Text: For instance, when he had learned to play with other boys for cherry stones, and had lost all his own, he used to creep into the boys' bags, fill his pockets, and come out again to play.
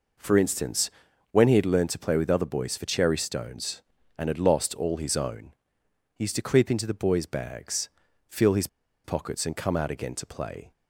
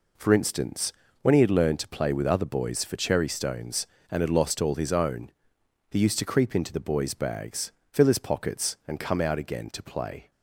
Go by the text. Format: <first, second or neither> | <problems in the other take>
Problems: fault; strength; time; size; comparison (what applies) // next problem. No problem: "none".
second | pauses between "his" and "pockets"; at 8.6 s; 0.37 s long